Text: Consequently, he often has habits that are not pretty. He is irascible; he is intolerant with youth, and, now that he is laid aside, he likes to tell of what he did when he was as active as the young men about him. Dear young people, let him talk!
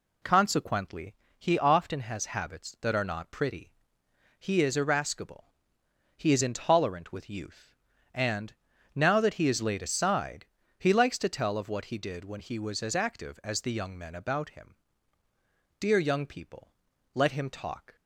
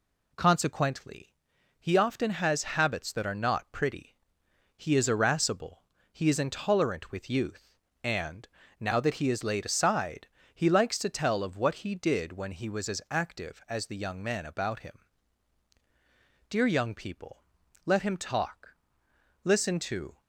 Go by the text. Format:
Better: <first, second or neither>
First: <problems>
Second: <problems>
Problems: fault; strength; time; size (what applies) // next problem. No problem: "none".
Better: first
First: none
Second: goes on to say "Listen to"; noticeable; from 19.4 s on; 0.78 s long